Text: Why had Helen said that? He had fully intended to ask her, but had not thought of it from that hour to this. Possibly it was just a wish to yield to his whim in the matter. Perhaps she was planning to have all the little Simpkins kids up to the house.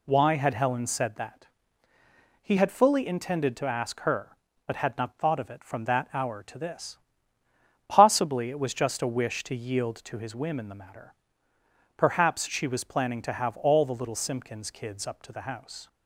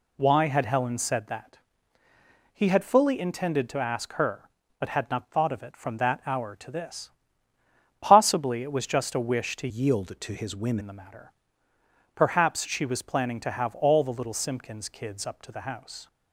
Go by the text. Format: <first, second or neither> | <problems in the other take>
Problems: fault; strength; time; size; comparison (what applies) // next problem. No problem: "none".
first | changes voice from "yield" to "whim"; from 9.6 to 10.7 s; 1.1 s long